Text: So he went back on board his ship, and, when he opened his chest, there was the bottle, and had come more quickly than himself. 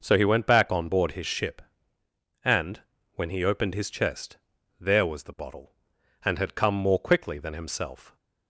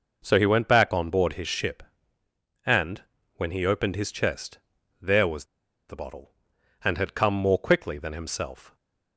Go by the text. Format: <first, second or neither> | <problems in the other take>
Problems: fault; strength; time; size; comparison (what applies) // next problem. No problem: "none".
first | pauses between "was" and "the"; at 5.4 s; 0.43 s long